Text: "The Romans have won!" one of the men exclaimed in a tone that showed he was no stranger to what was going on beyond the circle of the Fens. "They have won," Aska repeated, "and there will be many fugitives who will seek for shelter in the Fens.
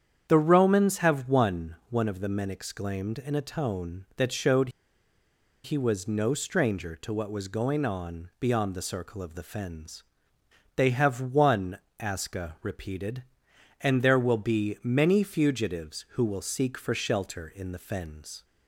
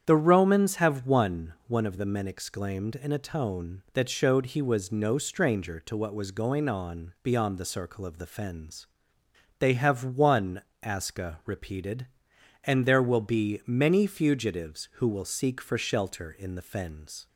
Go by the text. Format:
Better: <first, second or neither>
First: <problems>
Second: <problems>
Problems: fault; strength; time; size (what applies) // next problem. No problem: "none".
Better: second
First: starts louder than the rest; strong; until 1.3 s; 8.5 dB // pauses between "showed" and "he"; noticeable; at 4.6 s; 0.94 s long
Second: starts louder than the rest; strong; until 1.0 s; 8.5 dB